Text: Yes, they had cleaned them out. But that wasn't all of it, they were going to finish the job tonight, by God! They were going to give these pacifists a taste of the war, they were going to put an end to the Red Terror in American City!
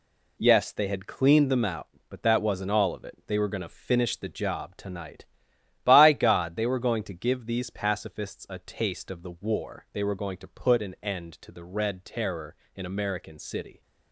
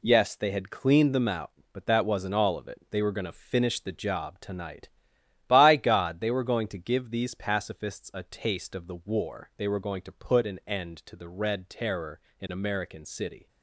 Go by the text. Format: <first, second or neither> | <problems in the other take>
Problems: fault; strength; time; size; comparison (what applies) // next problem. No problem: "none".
neither | none